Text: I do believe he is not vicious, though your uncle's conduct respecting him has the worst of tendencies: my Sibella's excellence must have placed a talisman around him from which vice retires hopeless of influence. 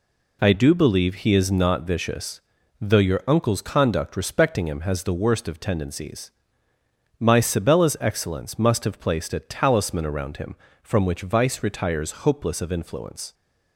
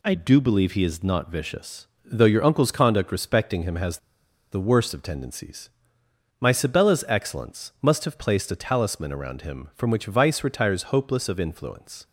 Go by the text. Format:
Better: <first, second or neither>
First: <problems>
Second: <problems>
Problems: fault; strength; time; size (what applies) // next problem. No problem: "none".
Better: first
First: none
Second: pauses between "has" and "the"; noticeable; at 3.9 s; 0.54 s long